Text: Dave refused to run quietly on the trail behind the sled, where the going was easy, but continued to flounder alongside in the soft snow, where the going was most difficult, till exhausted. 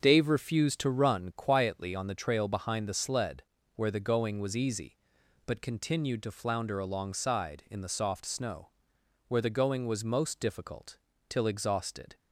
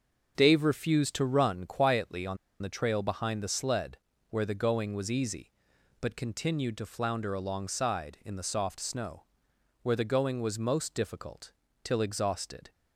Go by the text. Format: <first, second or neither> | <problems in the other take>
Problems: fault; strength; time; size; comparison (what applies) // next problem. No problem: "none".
first | starts louder than the rest; until 1.3 s; 6.5 dB; also in the first // pauses between "on" and "the"; slight; at 2.3 s; 0.24 s long